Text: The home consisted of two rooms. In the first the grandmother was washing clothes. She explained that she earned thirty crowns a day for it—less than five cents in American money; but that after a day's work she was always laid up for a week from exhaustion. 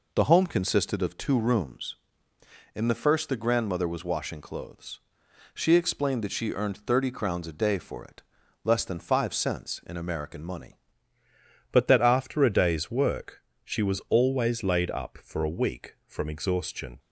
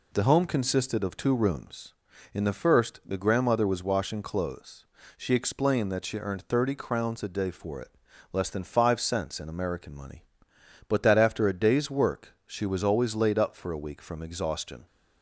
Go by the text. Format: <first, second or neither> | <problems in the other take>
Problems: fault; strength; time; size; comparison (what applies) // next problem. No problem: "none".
second | changes voice at "but"; from 11.7 s on; 5.2 s long // pauses between "work" and "she"; slight; at 13.4 s; 0.24 s long